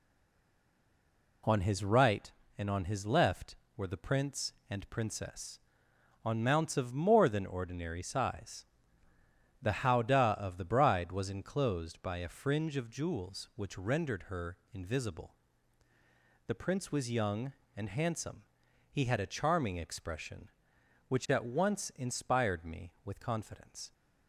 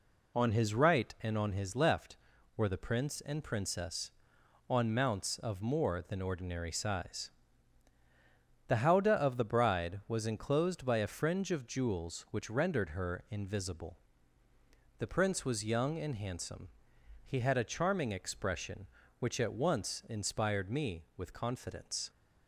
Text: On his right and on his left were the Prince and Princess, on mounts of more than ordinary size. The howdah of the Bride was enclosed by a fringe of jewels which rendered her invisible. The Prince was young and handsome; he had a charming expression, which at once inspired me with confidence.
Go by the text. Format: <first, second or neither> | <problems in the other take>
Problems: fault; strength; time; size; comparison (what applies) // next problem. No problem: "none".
second | stays silent before the first word; noticeable; until 1.4 s; 1.4 s long // pauses between "her" and "invisible"; slight; at 14.5 s; 0.16 s long